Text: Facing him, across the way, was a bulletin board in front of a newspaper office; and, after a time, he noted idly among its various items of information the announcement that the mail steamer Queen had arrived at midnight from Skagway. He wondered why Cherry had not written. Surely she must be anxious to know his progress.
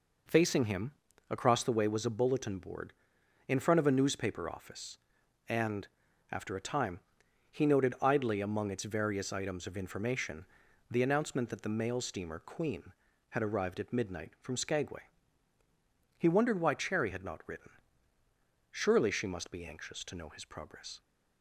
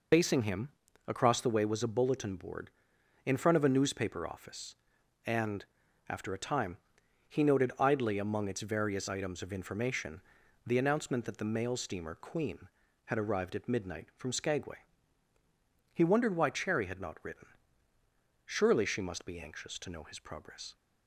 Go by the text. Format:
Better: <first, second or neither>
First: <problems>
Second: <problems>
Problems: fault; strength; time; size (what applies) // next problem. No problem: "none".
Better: first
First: pauses between "information" and "the"; noticeable; at 10.4 s; 0.46 s long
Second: loses the start of "Facing"; at 0.1 s; 75 ms // pauses between "information" and "the"; noticeable; at 10.2 s; 0.46 s long